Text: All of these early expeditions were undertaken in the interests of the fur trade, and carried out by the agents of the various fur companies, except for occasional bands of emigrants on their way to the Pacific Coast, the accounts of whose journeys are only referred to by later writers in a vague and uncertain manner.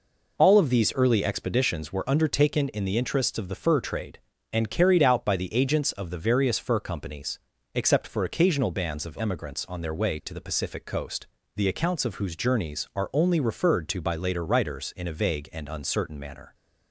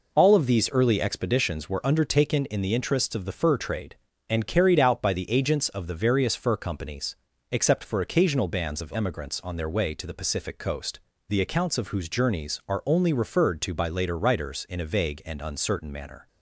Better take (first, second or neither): neither